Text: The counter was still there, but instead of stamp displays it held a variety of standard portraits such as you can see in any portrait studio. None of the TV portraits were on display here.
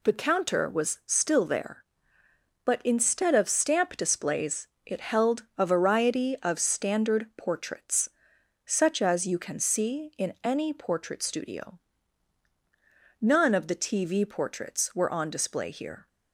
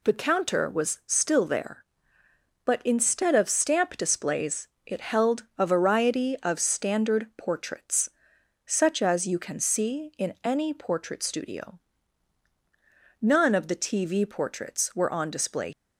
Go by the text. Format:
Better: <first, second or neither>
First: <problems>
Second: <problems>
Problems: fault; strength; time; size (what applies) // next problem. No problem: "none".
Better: first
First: pauses between "displays" and "it"; slight; at 4.6 s; 0.18 s long // pauses between "portraits" and "such"; noticeable; at 8.0 s; 0.56 s long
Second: pauses between "displays" and "it"; slight; at 4.6 s; 0.18 s long // pauses between "portraits" and "such"; noticeable; at 8.1 s; 0.56 s long // stops before "here"; at 15.7 s